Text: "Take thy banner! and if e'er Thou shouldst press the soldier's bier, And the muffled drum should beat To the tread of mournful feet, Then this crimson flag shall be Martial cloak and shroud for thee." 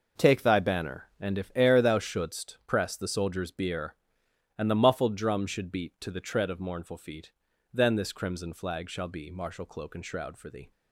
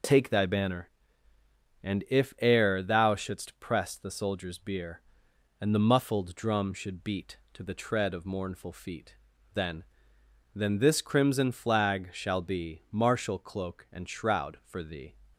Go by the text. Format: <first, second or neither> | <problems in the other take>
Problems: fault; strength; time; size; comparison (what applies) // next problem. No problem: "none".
first | says "Then" twice; at 10.5 s